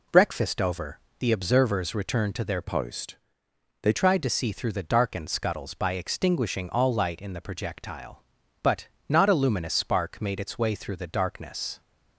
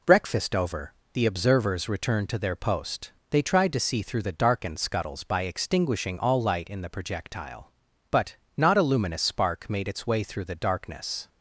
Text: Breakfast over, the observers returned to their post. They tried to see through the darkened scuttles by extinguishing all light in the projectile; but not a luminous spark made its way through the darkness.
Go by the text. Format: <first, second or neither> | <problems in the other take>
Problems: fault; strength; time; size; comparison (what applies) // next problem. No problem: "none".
second | changes voice from "post" to "They"; from 2.6 to 3.9 s; 1.3 s long // pauses between "but" and "not"; slight; at 8.8 s; 0.20 s long; slight in the second